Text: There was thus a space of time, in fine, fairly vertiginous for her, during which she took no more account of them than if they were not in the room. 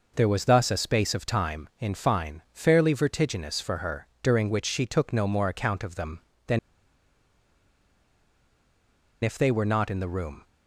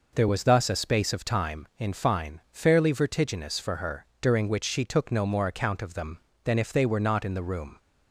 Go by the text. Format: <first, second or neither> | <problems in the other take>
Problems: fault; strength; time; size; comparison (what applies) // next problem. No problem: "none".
second | pauses between "than" and "if"; strong; at 6.5 s; 2.6 s long